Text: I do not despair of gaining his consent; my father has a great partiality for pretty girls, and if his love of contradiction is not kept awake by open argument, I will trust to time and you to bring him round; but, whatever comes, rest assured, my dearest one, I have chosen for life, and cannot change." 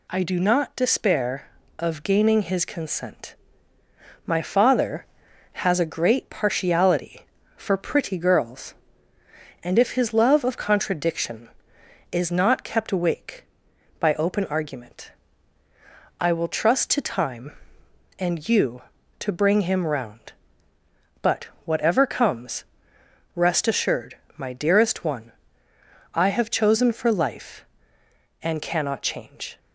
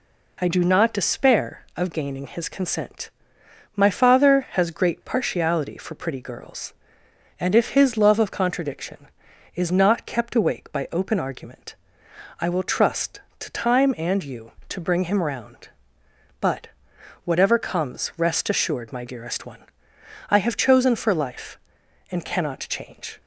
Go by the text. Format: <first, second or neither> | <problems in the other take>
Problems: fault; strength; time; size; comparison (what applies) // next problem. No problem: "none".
first | skips "a"; at 4.7 s